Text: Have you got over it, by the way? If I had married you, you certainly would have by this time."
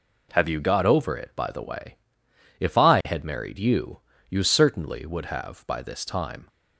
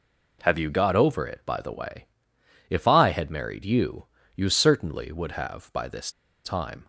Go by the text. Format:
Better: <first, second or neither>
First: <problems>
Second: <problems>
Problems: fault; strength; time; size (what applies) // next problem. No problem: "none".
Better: first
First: none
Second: pauses between "this" and "time"; slight; at 6.0 s; 0.34 s long